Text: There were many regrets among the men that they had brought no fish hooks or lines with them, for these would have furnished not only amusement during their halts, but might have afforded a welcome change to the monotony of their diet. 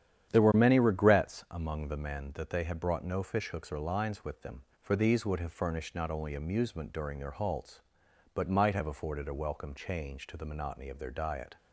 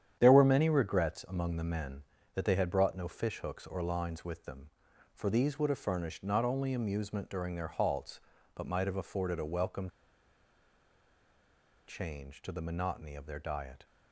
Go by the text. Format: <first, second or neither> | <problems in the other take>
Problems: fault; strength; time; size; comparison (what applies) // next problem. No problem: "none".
first | starts louder than the rest; strong; until 1.2 s; 9.5 dB; strong in the first // pauses between "welcome" and "change"; strong; at 9.8 s; 1.9 s long